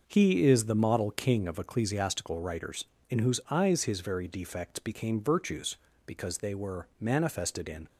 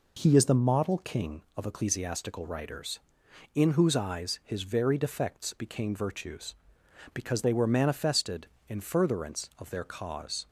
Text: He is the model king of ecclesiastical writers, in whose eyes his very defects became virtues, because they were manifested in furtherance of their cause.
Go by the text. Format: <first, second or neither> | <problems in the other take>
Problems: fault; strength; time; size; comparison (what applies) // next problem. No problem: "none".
second | stops before "furtherance of their cause"; at 7.8 s